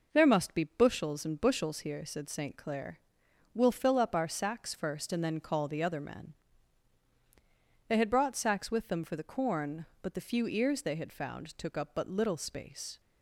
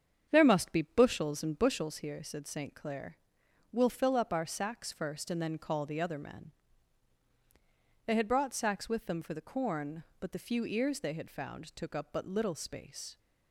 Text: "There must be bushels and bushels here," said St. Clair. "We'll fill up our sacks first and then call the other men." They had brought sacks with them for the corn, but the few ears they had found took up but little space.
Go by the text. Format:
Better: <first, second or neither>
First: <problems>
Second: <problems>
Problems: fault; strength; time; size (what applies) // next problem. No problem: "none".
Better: first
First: none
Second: starts louder than the rest; strong; until 1.8 s; 8 dB